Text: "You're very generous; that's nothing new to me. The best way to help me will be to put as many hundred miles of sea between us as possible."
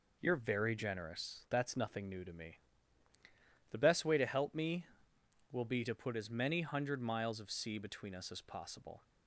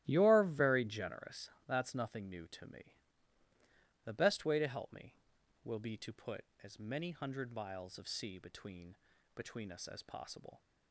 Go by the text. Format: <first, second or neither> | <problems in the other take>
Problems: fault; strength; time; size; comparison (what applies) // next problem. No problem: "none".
first | starts louder than the rest; strong; until 1.0 s; 15 dB // says "between" twice; at 9.3 s